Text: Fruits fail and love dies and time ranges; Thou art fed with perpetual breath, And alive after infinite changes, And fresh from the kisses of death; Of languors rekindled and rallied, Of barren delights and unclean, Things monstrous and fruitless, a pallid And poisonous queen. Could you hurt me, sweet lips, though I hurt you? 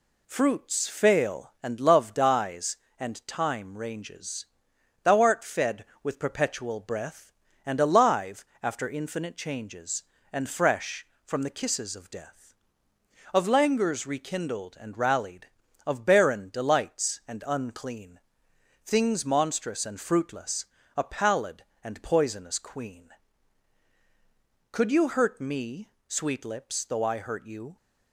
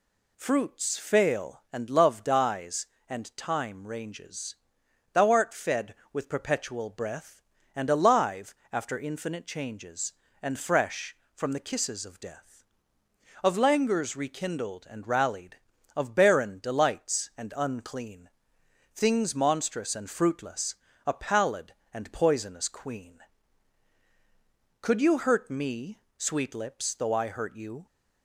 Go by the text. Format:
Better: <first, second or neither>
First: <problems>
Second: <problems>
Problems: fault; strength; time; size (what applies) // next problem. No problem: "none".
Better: second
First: gets quieter; slight; throughout; 3.5 dB // pauses between "alive" and "after"; slight; at 8.4 s; 0.18 s long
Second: pauses between "alive" and "after"; slight; at 8.5 s; 0.18 s long